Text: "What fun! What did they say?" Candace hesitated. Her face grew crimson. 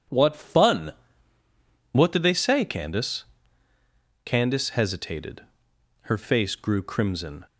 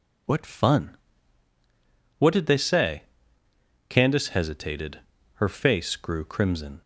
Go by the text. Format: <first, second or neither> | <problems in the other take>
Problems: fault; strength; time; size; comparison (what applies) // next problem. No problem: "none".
second | says "Candace" twice; at 4.2 s